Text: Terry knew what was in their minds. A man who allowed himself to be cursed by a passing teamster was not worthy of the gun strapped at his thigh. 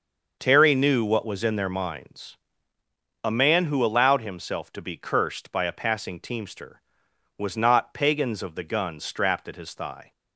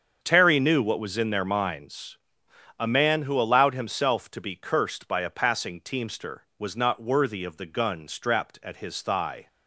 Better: second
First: starts louder than the rest; noticeable; until 1.4 s; 6 dB // says "pagans" for "worthy"; at 7.9 s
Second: starts louder than the rest; strong; until 1.2 s; 7 dB

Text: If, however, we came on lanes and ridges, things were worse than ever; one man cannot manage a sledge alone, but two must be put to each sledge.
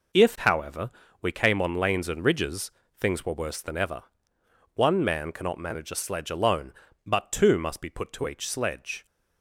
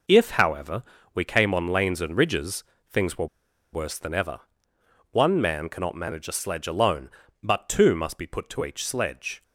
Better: first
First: none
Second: pauses between "were" and "worse"; noticeable; at 3.2 s; 0.46 s long

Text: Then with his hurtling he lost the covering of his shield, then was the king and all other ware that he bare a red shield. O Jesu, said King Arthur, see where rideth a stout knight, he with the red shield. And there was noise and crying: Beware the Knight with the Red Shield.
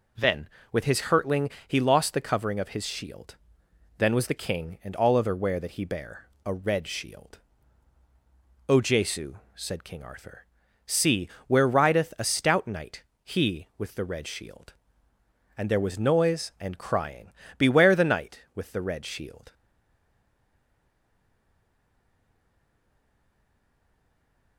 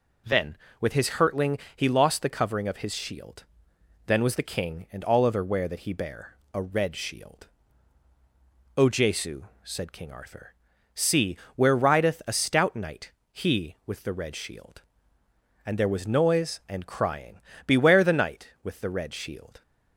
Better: second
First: pauses between "hurtling" and "he"; slight; at 1.4 s; 0.18 s long // pauses between "bare" and "a"; slight; at 6.2 s; 0.18 s long // pauses between "see" and "where"; slight; at 11.2 s; 0.20 s long // stays silent after the last word; strong; from 19.5 s on; 5.0 s long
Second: pauses between "hurtling" and "he"; slight; at 1.5 s; 0.18 s long // pauses between "bare" and "a"; slight; at 6.3 s; 0.18 s long // pauses between "see" and "where"; slight; at 11.3 s; 0.20 s long

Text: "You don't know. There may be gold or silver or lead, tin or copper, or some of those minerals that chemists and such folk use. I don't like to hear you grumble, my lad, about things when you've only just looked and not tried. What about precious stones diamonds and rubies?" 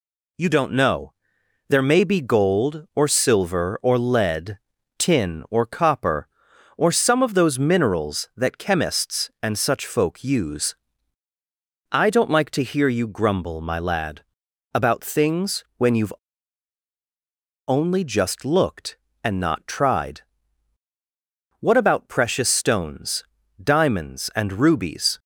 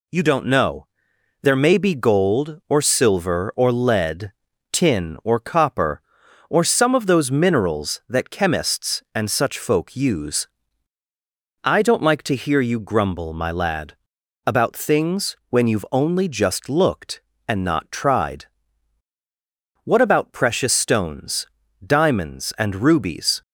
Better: second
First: pauses between "you've" and "only"; strong; at 16.1 s; 1.5 s long // pauses between "stones" and "diamonds"; at 23.2 s; 0.38 s long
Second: pauses between "stones" and "diamonds"; at 21.4 s; 0.38 s long

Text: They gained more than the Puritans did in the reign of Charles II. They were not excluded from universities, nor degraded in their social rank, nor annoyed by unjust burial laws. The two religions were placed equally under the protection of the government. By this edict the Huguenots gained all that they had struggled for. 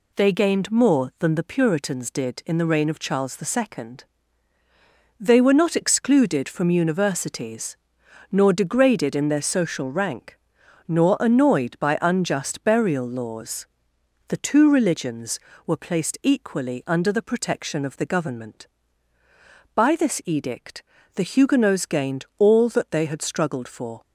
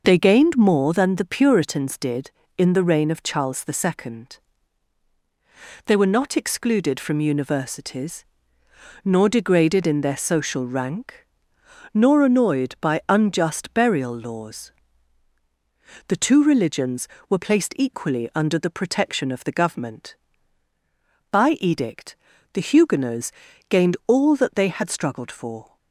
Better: first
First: pauses between "edict" and "the"; slight; at 20.8 s; 0.32 s long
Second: skips "this"; at 21.5 s // pauses between "edict" and "the"; at 22.1 s; 0.38 s long // pauses between "Huguenots" and "gained"; at 23.3 s; 0.38 s long

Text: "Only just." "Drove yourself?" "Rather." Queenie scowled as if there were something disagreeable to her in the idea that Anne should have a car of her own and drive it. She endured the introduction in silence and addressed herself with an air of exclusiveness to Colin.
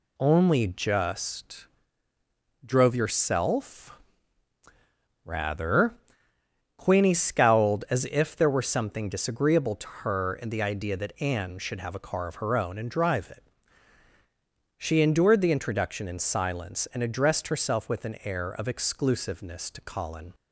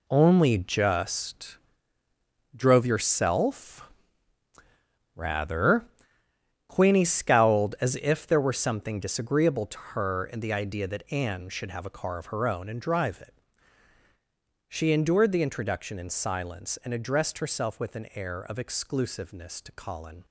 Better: first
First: none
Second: gets quieter; strong; throughout; 10 dB

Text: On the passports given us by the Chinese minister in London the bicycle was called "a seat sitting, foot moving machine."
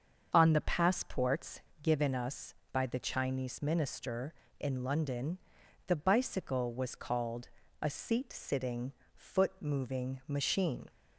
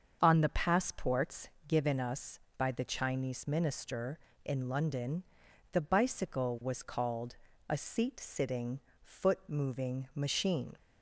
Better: neither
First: starts louder than the rest; until 1.3 s; 7 dB // pauses between "passports" and "given"; slight; at 1.5 s; 0.20 s long // pauses between "London" and "the"; noticeable; at 5.3 s; 0.48 s long // pauses between "called" and "a"; slight; at 7.4 s; 0.34 s long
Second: starts louder than the rest; until 1.2 s; 7 dB // pauses between "passports" and "given"; slight; at 1.4 s; 0.18 s long // pauses between "London" and "the"; noticeable; at 5.2 s; 0.48 s long // pauses between "called" and "a"; slight; at 7.3 s; 0.34 s long

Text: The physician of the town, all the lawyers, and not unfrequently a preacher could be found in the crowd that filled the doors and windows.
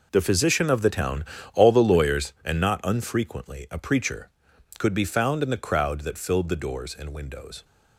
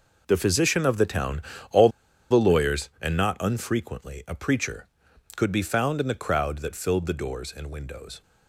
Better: first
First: none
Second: pauses between "all" and "the"; at 1.8 s; 0.43 s long

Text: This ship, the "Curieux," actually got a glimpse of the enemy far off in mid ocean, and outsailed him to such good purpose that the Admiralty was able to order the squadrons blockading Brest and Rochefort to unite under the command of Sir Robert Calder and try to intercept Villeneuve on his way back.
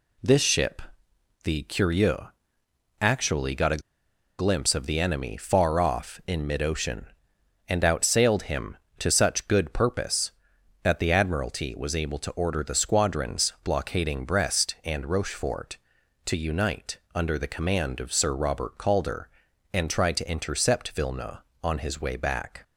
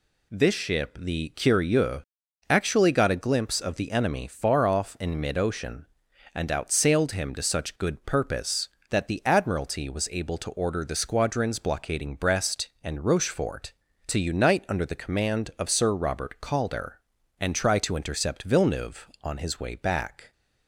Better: second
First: pauses between "a" and "glimpse"; noticeable; at 3.8 s; 0.59 s long // pauses between "unite" and "under"; slight; at 16.9 s; 0.18 s long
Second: none

